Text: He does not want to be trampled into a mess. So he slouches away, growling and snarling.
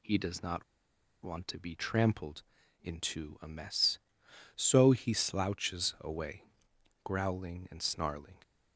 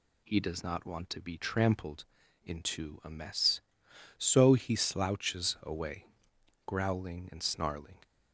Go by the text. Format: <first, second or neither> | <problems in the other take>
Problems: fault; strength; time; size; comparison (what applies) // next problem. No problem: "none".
second | pauses between "not" and "want"; noticeable; at 0.6 s; 0.60 s long // pauses between "trampled" and "into"; at 2.4 s; 0.40 s long; also in the second